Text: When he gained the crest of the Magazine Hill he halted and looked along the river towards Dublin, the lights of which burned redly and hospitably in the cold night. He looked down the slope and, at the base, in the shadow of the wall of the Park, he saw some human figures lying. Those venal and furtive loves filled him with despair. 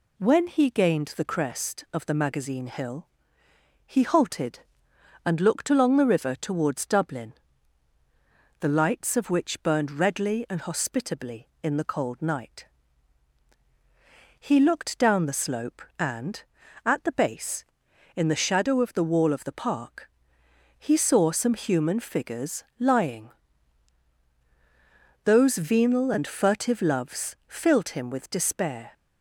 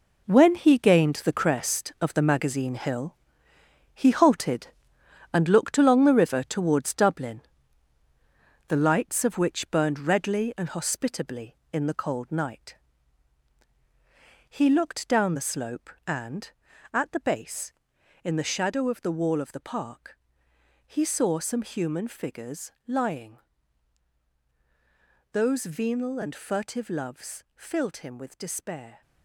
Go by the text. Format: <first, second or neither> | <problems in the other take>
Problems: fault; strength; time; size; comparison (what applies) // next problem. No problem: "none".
first | gets quieter; strong; throughout; 9.5 dB // pauses between "Hill" and "he"; noticeable; at 3.1 s; 0.80 s long; noticeable in the first // pauses between "figures" and "lying"; slight; at 22.7 s; 0.16 s long; slight in the first